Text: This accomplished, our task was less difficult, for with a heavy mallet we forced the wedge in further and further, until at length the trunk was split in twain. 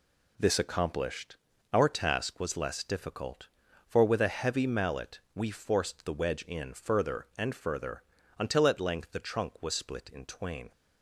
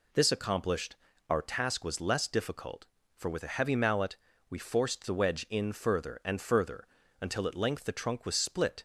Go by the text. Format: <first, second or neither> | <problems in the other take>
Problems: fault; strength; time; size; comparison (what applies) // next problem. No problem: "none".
first | pauses between "mallet" and "we"; slight; at 4.1 s; 0.32 s long // stops before "in twain"; at 8.7 s